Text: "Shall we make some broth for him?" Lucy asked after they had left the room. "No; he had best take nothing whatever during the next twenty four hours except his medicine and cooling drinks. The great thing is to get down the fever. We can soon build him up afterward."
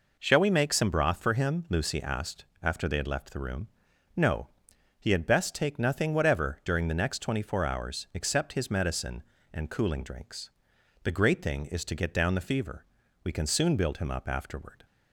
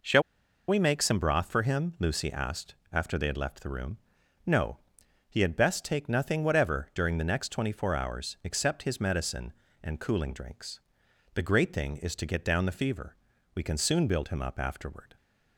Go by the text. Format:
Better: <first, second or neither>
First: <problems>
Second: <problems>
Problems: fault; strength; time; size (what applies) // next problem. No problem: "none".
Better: first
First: pauses between "asked" and "after"; slight; at 2.4 s; 0.18 s long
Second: pauses between "Shall" and "we"; noticeable; at 0.2 s; 0.46 s long // pauses between "asked" and "after"; slight; at 2.7 s; 0.18 s long